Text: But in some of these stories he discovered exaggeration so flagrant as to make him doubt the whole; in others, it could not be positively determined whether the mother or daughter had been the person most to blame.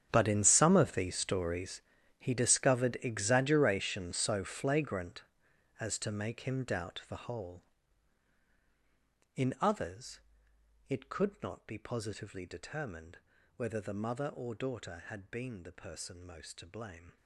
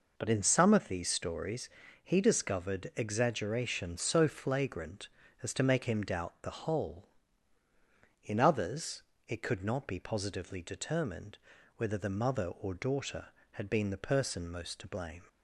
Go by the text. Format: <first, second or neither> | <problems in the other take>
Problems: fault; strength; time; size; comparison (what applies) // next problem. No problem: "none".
second | gets quieter; strong; throughout; 17 dB // pauses between "stories" and "he"; slight; at 1.8 s; 0.36 s long; slight in the second // pauses between "determined" and "whether"; at 13.1 s; 0.38 s long; also in the second